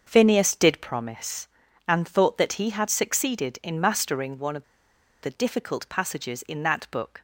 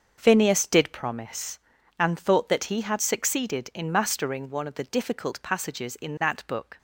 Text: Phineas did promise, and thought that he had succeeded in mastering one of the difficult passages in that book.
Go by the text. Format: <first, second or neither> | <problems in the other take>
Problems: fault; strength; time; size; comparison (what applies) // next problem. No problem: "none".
second | starts louder than the rest; until 1.0 s; 6.5 dB; also in the second // pauses between "of" and "the"; noticeable; at 4.6 s; 0.59 s long